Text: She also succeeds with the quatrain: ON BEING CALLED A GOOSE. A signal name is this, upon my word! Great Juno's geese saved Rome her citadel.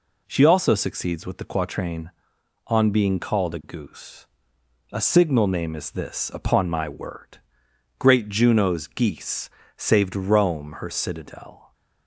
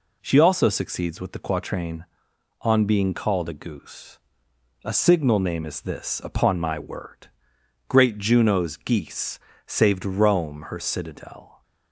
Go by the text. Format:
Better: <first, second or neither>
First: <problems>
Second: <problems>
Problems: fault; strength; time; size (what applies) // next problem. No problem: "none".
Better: neither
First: pauses between "geese" and "saved"; slight; at 9.4 s; 0.28 s long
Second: pauses between "geese" and "saved"; slight; at 9.3 s; 0.28 s long